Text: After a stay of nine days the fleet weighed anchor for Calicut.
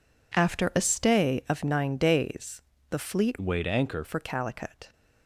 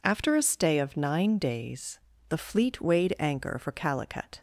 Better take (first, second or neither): second